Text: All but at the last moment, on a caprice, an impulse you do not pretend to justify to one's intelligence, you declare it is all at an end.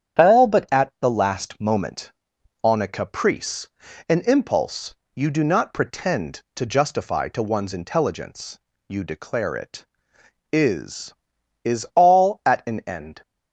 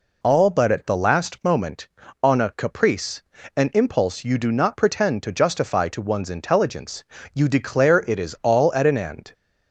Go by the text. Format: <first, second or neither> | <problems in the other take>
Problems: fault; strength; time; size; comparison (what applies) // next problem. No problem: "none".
second | starts louder than the rest; strong; until 1.3 s; 8.5 dB // pauses between "impulse" and "you"; slight; at 4.9 s; 0.18 s long // says "is" twice; at 11.6 s